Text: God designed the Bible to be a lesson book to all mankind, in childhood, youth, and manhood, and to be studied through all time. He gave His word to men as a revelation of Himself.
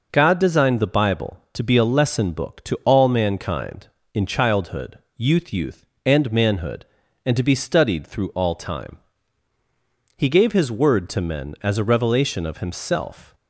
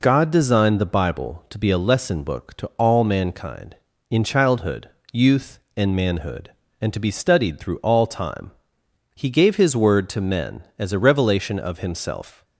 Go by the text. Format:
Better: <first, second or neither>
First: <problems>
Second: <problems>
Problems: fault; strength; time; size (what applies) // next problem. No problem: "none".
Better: second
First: says "youth" twice; at 5.5 s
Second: none